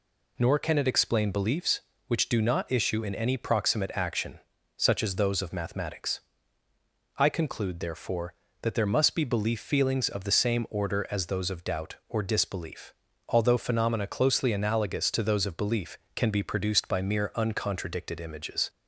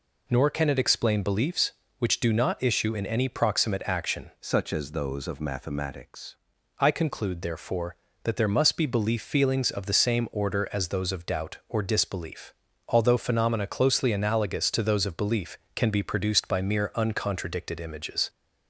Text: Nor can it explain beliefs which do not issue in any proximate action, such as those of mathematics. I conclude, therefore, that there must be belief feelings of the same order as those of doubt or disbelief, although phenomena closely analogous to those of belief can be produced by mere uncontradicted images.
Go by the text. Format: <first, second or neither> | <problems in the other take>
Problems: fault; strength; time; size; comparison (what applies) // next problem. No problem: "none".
first | changes voice from "such" to "mathematics"; from 4.3 to 6.3 s; 2.0 s long